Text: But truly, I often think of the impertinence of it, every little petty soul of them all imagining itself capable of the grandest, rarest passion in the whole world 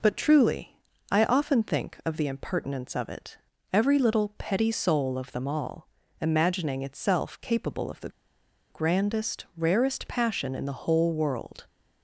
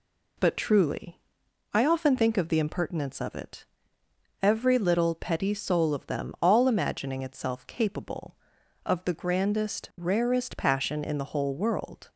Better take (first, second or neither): second